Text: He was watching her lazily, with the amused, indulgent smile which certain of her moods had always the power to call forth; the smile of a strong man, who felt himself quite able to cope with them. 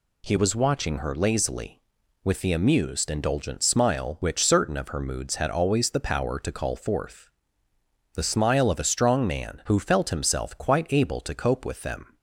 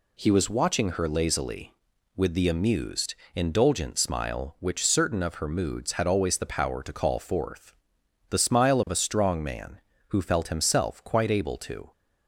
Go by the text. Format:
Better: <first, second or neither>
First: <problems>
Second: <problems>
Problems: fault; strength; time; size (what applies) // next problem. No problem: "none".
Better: first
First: none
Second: stops before "cope with them"; at 11.9 s